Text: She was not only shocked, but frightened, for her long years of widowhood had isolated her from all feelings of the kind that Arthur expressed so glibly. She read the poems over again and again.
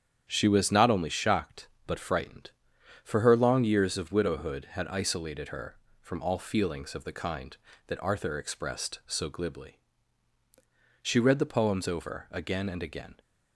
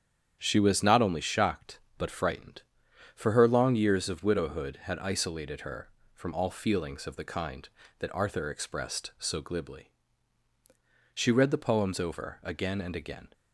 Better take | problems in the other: neither | starts louder than the rest; strong; the same in both

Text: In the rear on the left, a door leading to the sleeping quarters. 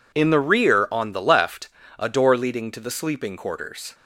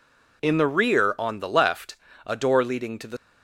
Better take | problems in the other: first | stops before "sleeping quarters"; at 3.1 s

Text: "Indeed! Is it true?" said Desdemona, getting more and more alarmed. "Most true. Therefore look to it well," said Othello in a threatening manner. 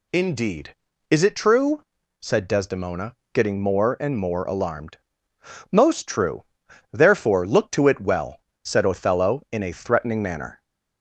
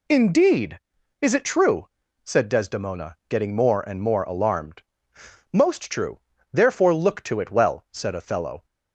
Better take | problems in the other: first | stops before "in a threatening manner"; at 8.6 s

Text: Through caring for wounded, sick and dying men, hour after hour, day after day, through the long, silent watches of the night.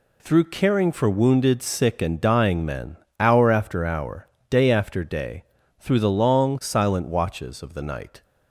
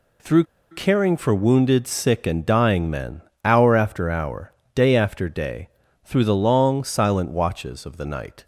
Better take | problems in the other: first | pauses between "Through" and "caring"; slight; at 0.4 s; 0.26 s long

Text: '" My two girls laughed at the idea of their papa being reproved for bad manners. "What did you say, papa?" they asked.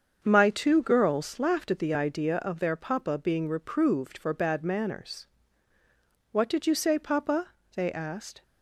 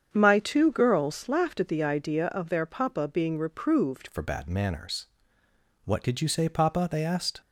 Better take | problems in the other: first | starts louder than the rest; strong; until 1.1 s; 7.5 dB; also in the first // changes voice at "for"; from 4.1 s on; 3.3 s long

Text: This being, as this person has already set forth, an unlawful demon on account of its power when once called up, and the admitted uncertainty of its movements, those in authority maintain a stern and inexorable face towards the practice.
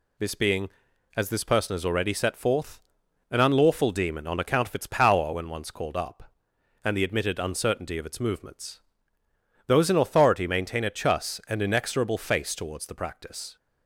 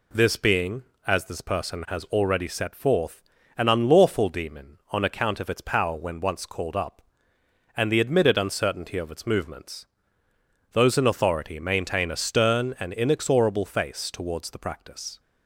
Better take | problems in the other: second | says "chus" for "stern"; at 10.9 s

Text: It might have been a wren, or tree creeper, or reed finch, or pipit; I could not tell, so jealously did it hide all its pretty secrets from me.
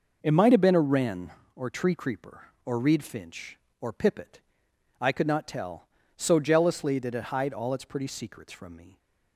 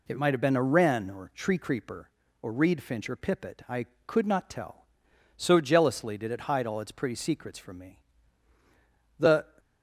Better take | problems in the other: first | goes on to say "The"; slight; from 9.1 s on; 0.26 s long

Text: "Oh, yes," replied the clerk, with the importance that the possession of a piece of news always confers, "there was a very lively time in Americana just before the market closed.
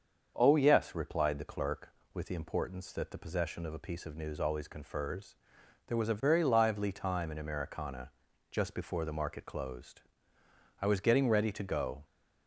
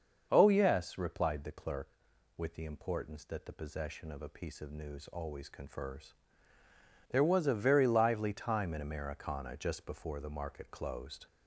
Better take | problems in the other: second | starts louder than the rest; until 1.3 s; 7 dB; also in the second // pauses between "Americana" and "just"; at 8.1 s; 0.40 s long // goes on to say "I was getting ready to go"; noticeable; from 10.7 s on; 1.2 s long

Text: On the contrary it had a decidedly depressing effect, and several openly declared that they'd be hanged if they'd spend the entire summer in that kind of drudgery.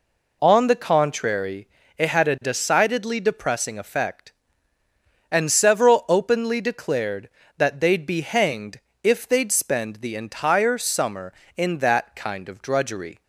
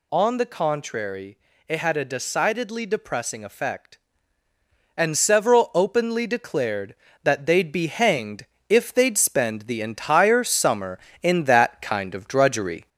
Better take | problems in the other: first | gets louder; slight; throughout; 2 dB // pauses between "contrary" and "it"; slight; at 1.3 s; 0.30 s long; slight in the first // pauses between "hanged" and "if"; slight; at 8.4 s; 0.24 s long; slight in the first

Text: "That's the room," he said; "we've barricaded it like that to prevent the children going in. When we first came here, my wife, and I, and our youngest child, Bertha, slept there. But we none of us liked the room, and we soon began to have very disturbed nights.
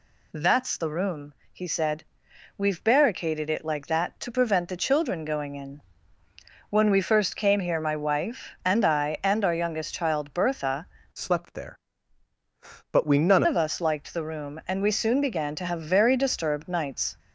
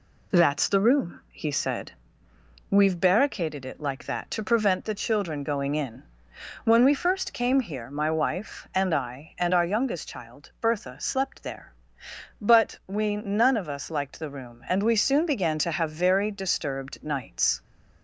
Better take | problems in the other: second | changes voice from "slept" to "none"; from 11.1 to 13.4 s; 2.3 s long

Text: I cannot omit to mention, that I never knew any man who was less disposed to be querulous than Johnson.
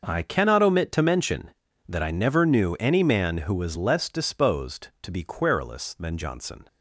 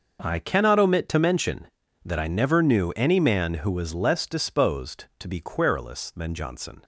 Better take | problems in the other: neither | starts louder than the rest; noticeable; the same in both

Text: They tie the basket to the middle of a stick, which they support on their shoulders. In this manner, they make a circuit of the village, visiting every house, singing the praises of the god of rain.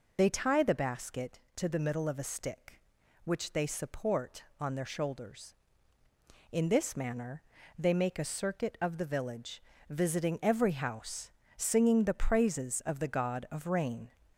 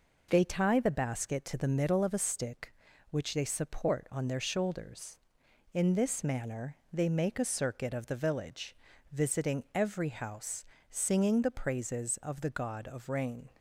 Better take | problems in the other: second | loses the start of "They"; at 0.1 s; 55 ms

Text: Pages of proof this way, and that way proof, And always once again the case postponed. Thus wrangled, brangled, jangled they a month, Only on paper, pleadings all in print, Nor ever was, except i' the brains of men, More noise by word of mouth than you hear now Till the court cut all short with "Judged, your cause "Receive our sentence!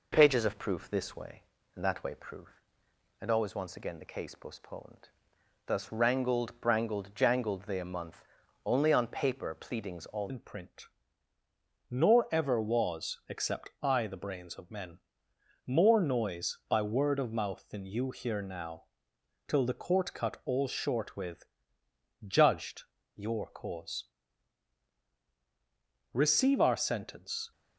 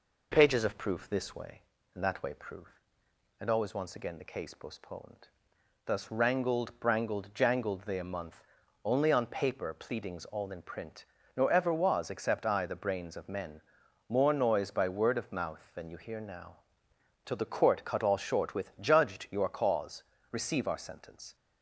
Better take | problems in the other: second | changes voice at "in"; from 10.2 s on; 17.3 s long // pauses between "now" and "Till"; noticeable; at 18.8 s; 0.60 s long; noticeable in the second // pauses between "with" and "Judged"; noticeable; at 21.4 s; 0.82 s long // pauses between "cause" and "Receive"; strong; at 24.0 s; 2.0 s long; slight in the second

